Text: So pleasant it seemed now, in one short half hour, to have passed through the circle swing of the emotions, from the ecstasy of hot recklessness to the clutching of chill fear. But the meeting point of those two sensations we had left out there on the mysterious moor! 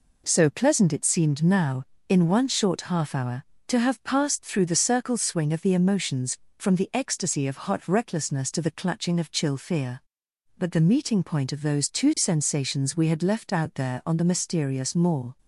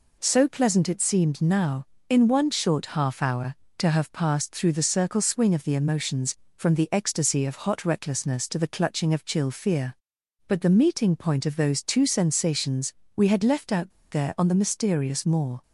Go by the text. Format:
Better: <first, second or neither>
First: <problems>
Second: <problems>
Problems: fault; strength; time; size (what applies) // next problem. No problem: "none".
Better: first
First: none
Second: pauses between "sensations" and "we"; slight; at 12.9 s; 0.24 s long // pauses between "out" and "there"; slight; at 13.9 s; 0.20 s long